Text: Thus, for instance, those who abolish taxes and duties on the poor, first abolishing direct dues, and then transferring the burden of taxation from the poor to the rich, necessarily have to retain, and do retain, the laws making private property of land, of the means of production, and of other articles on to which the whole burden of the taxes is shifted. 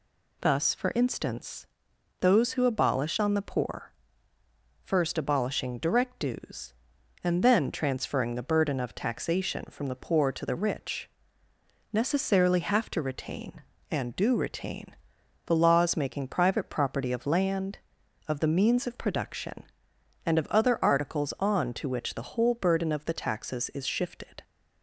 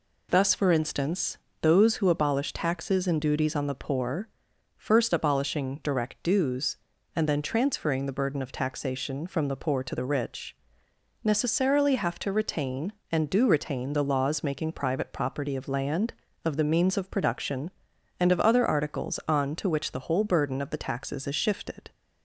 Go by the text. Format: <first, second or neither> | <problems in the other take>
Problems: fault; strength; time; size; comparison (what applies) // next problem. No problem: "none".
second | skips "taxes and duties"; at 3.1 s